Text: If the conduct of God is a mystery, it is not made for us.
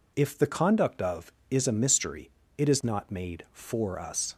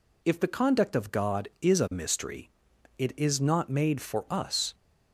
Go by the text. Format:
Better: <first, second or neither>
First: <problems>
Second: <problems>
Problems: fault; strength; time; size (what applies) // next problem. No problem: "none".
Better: second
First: skips "God"; at 1.4 s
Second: none